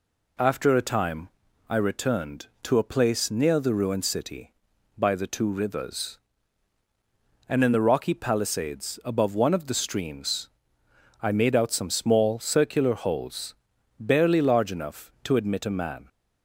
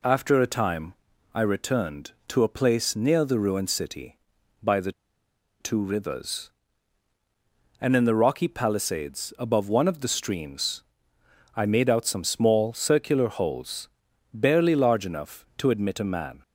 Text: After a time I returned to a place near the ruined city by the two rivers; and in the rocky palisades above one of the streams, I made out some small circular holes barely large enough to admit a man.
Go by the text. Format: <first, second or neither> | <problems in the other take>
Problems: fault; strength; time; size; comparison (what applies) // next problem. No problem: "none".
first | pauses between "time" and "I"; at 0.9 s; 0.40 s long; also in the first // pauses between "the" and "two"; noticeable; at 4.9 s; 0.68 s long // pauses between "holes" and "barely"; noticeable; at 13.8 s; 0.46 s long; noticeable in the first